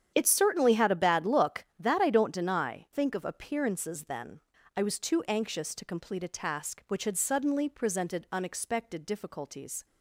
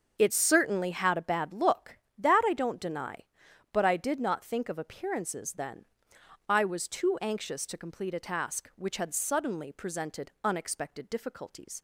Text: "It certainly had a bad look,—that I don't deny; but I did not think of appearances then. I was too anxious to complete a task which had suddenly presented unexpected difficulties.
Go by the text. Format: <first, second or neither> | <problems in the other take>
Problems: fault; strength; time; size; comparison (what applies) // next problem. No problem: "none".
second | starts louder than the rest; strong; until 1.1 s; 9 dB; also in the second // skips "but I did not"; at 2.9 s